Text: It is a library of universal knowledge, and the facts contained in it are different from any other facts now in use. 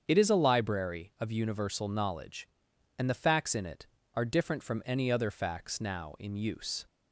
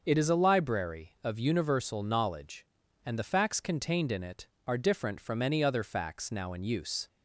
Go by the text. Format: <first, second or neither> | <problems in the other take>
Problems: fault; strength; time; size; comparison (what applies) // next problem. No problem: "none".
second | starts louder than the rest; strong; until 1.0 s; 7.5 dB; also in the second // skips "contained"; at 3.5 s